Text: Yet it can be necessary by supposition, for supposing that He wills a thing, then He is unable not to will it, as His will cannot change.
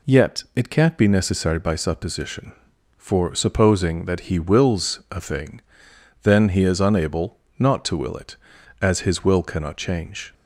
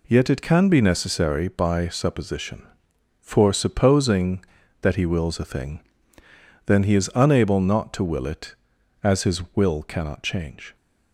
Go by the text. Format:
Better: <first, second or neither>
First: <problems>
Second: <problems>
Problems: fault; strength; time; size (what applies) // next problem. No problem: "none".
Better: second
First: says "can't" for "can"; at 0.6 s // pauses between "unable" and "not"; slight; at 7.3 s; 0.22 s long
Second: none